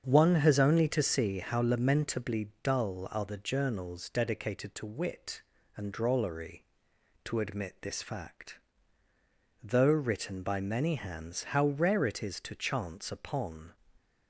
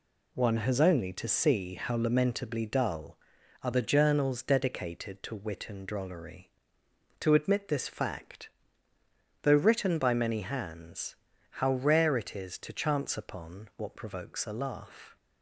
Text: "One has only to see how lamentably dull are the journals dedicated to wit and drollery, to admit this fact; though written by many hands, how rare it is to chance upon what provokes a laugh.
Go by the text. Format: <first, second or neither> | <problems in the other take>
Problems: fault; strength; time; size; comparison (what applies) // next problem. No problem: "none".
second | starts louder than the rest; strong; until 1.0 s; 7.5 dB // stops before "what provokes a laugh"; at 13.9 s